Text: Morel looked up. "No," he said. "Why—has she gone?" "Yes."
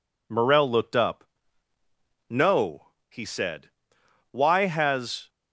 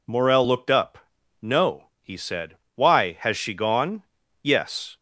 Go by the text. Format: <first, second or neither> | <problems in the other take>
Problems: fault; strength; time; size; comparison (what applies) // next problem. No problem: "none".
second | stops before "she gone Yes"; at 5.2 s